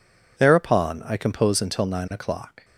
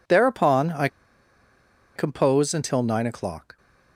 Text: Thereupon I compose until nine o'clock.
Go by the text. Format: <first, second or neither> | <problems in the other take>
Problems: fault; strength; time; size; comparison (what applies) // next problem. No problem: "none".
first | pauses between "I" and "compose"; at 0.8 s; 1.0 s long